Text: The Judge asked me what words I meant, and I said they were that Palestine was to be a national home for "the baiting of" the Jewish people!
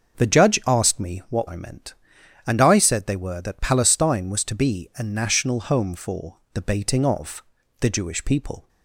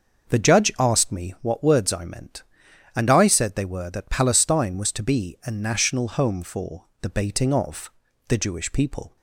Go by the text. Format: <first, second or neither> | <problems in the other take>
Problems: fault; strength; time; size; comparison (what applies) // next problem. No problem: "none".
second | starts louder than the rest; until 1.2 s; 6.5 dB; also in the second // skips "words"; at 1.4 s // pauses between "for" and "the"; slight; at 6.3 s; 0.16 s long; slight in the second // pauses between "of" and "the"; slight; at 7.4 s; 0.34 s long; slight in the second